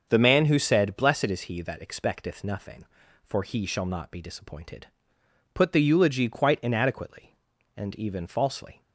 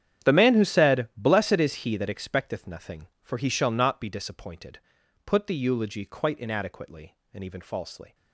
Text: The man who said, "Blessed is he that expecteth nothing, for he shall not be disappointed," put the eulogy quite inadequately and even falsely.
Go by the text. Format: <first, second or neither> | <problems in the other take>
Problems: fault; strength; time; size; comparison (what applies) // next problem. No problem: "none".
first | gets quieter; strong; throughout; 17.5 dB // starts louder than the rest; strong; until 1.3 s; 9.5 dB; also in the first